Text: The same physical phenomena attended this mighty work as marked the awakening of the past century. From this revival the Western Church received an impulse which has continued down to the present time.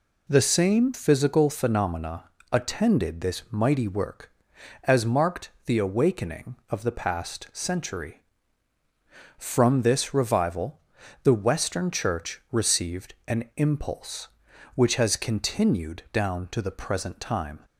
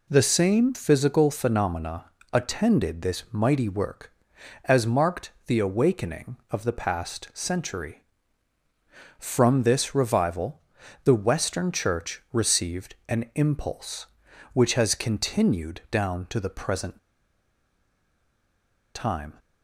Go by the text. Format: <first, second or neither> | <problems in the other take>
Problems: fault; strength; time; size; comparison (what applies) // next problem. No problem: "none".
first | pauses between "phenomena" and "attended"; slight; at 2.0 s; 0.28 s long; slight in the first // pauses between "revival" and "the"; at 10.6 s; 0.44 s long; also in the first // pauses between "present" and "time"; strong; at 16.9 s; 1.9 s long